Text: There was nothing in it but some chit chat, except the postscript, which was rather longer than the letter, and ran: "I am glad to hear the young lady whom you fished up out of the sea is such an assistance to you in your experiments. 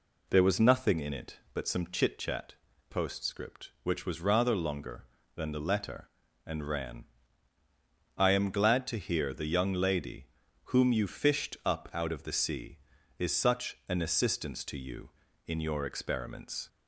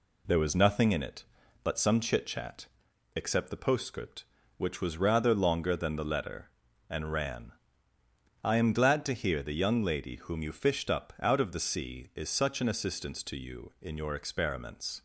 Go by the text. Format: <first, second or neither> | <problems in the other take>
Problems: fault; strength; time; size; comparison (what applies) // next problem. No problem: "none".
second | skips "except the"; at 2.7 s // pauses between "lady" and "whom"; at 10.2 s; 0.38 s long